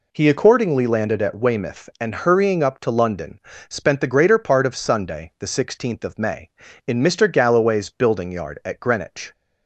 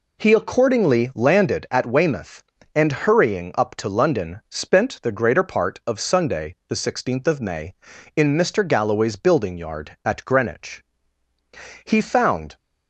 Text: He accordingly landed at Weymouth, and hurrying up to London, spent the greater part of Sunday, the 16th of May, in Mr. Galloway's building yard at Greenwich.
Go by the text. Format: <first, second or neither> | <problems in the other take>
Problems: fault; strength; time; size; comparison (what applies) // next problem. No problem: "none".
first | goes on to say "He found"; noticeable; from 11.8 s on; 0.70 s long